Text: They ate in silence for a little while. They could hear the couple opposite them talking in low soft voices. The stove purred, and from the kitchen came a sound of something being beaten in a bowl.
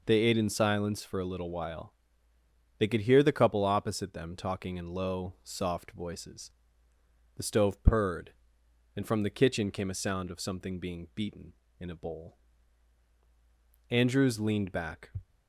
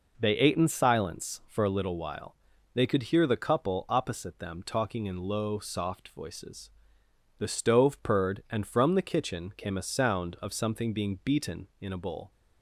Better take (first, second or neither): second